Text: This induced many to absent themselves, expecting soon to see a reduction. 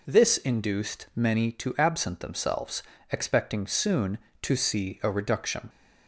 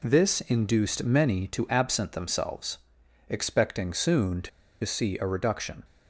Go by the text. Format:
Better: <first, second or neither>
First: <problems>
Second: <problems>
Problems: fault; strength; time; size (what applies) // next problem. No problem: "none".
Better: first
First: none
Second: pauses between "to" and "see"; slight; at 4.4 s; 0.34 s long